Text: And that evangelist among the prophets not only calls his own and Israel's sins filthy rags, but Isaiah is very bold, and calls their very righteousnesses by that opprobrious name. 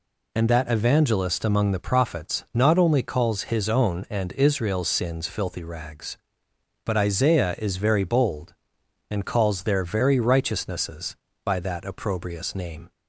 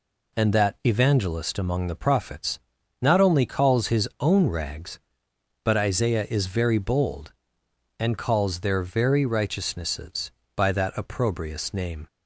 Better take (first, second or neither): first